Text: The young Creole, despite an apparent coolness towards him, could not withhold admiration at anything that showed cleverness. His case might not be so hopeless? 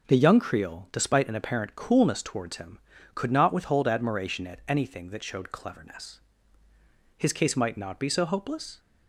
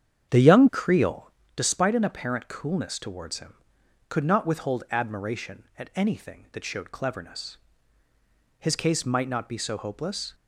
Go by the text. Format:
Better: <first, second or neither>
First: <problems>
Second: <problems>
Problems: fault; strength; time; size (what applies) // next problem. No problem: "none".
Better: first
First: none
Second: starts louder than the rest; strong; until 1.5 s; 9 dB